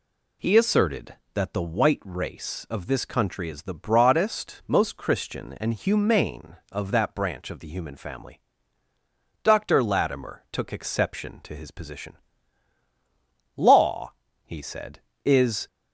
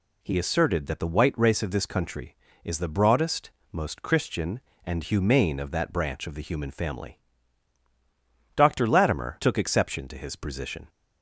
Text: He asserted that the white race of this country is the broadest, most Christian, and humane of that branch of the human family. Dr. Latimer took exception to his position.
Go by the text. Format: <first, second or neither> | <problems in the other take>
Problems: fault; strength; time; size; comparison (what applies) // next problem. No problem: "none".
second | goes on to say "Law he said is"; strong; from 13.5 s on; 2.1 s long